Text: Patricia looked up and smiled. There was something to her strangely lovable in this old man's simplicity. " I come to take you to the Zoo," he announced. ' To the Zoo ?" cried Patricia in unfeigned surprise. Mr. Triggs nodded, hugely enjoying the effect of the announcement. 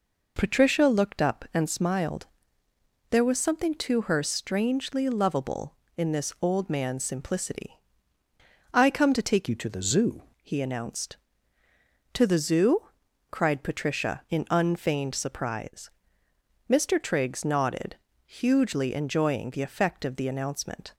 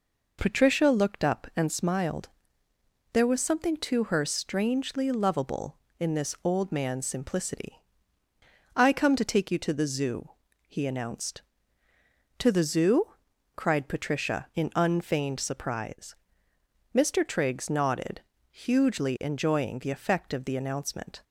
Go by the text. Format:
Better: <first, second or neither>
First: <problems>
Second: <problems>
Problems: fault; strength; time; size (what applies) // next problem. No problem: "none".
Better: second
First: changes voice from "you" to "Zoo"; from 9.4 to 10.2 s; 0.8 s long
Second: none